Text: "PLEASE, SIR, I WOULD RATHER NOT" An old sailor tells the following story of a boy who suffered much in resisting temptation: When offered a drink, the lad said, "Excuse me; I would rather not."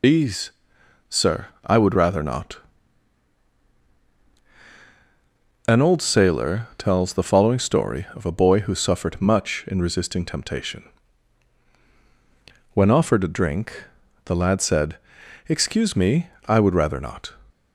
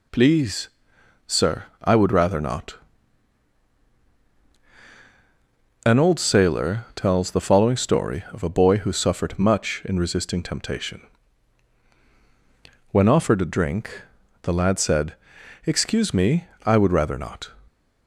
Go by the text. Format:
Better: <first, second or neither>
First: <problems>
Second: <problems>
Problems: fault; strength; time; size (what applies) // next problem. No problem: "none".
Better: second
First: loses the start of "PLEASE"; at 0.0 s; 105 ms // pauses between "NOT" and "An"; strong; at 2.5 s; 3.0 s long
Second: pauses between "NOT" and "An"; strong; at 2.7 s; 3.0 s long